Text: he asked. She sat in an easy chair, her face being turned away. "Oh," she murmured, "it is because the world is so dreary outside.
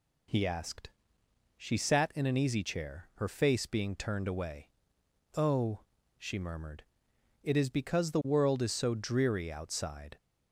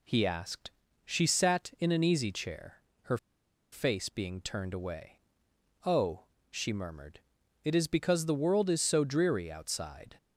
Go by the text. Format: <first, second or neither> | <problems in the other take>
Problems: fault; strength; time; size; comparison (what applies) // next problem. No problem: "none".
first | pauses between "her" and "face"; noticeable; at 3.1 s; 0.55 s long